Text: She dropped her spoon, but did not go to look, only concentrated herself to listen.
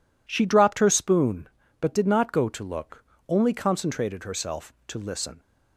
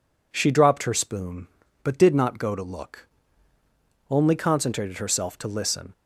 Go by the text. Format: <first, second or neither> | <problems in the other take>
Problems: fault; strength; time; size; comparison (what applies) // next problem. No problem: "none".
neither | none